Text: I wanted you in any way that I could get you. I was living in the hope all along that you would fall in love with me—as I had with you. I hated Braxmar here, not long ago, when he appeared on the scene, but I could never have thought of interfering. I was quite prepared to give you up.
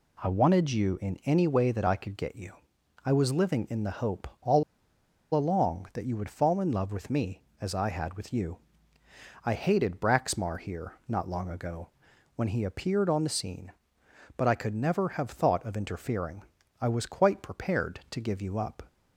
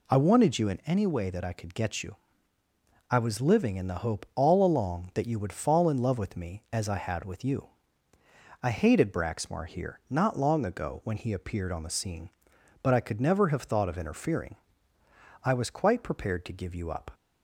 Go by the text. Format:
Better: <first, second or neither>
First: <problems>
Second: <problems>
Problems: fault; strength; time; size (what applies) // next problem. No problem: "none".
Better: second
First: pauses between "hope" and "all"; slight; at 4.2 s; 0.16 s long // pauses between "all" and "along"; noticeable; at 4.6 s; 0.71 s long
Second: none